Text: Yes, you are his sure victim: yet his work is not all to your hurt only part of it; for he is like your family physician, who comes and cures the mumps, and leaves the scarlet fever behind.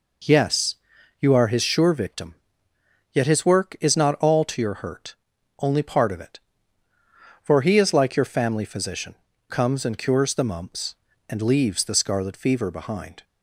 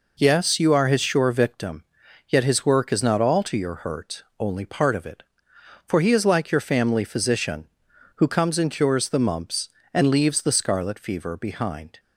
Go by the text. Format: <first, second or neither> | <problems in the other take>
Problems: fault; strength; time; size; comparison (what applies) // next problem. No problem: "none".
second | pauses between "hurt" and "only"; at 5.1 s; 0.44 s long; slight in the second // skips "who"; at 9.3 s